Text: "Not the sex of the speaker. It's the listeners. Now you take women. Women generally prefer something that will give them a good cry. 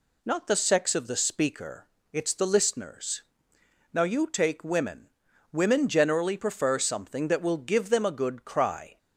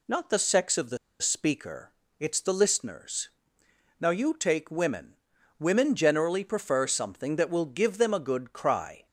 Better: first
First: none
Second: pauses between "the" and "speaker"; slight; at 0.9 s; 0.24 s long

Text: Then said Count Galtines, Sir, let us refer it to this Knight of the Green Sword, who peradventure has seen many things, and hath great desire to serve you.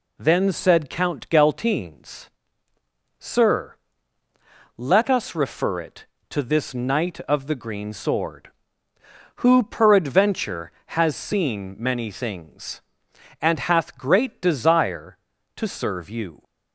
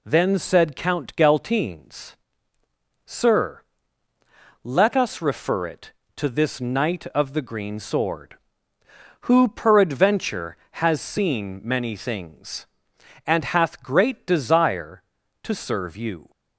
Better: neither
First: none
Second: none

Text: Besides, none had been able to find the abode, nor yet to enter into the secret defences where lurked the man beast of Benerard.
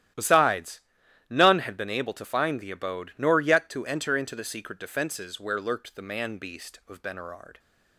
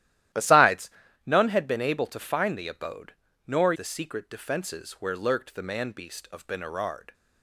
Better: first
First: starts louder than the rest; strong; until 1.6 s; 12.5 dB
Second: starts louder than the rest; strong; until 1.6 s; 13.5 dB // skips "yet to enter into"; at 3.7 s

